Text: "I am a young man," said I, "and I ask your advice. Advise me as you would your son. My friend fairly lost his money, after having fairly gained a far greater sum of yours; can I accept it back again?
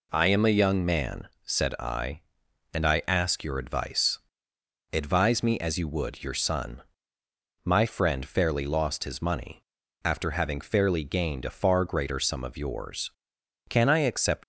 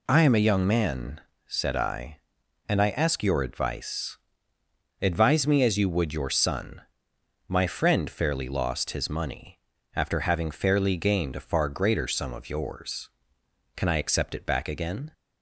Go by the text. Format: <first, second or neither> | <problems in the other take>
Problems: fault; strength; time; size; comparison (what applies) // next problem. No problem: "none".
second | stops before "it back again"; at 14.4 s